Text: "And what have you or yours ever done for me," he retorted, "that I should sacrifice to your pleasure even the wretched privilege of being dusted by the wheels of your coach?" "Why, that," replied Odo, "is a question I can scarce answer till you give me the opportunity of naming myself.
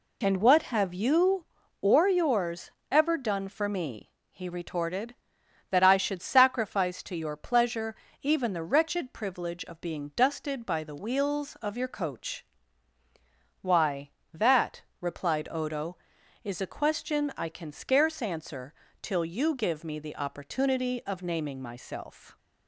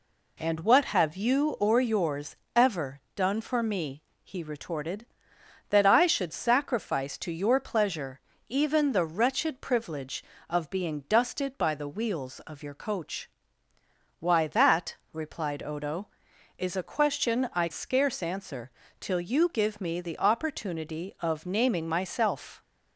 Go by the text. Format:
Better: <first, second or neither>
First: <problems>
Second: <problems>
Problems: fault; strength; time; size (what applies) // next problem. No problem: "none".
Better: first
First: pauses between "yours" and "ever"; slight; at 2.6 s; 0.22 s long // pauses between "pleasure" and "even"; slight; at 7.9 s; 0.26 s long // pauses between "answer" and "till"; slight; at 18.7 s; 0.26 s long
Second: pauses between "yours" and "ever"; slight; at 2.3 s; 0.18 s long // pauses between "ever" and "done"; slight; at 3.0 s; 0.16 s long // pauses between "pleasure" and "even"; slight; at 8.2 s; 0.28 s long // skips "can"; at 17.6 s // pauses between "answer" and "till"; slight; at 18.7 s; 0.28 s long